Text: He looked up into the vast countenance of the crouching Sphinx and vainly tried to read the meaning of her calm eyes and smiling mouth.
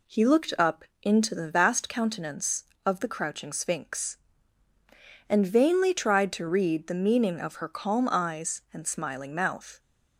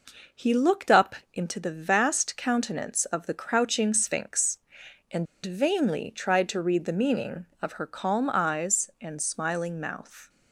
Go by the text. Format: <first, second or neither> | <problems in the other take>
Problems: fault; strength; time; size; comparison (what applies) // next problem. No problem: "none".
first | pauses between "up" and "into"; slight; at 1.1 s; 0.18 s long; slight in the first // pauses between "and" and "vainly"; slight; at 5.2 s; 0.18 s long